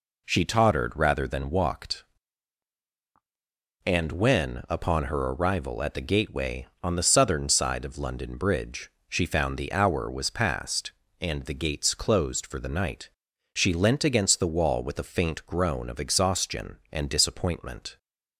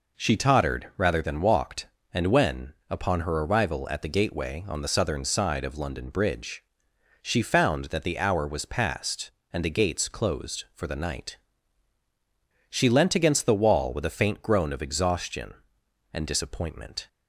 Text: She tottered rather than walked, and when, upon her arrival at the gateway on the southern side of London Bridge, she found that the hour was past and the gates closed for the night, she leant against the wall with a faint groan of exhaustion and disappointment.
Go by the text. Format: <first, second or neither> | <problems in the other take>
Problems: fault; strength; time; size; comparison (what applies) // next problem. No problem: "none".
second | skips "that"; at 9.5 s